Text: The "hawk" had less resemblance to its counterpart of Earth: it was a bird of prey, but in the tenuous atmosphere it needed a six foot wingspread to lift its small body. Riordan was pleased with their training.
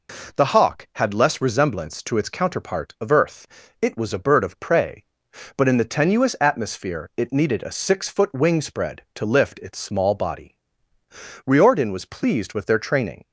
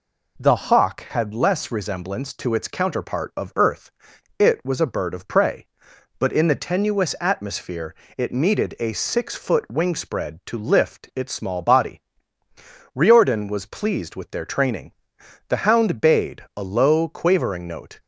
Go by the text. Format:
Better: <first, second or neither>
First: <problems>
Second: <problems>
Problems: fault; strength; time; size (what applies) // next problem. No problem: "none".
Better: first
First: none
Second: pauses between "atmosphere" and "it"; slight; at 7.9 s; 0.24 s long // goes on to say "The hound bayed a low quavering note"; strong; from 15.4 s on; 2.5 s long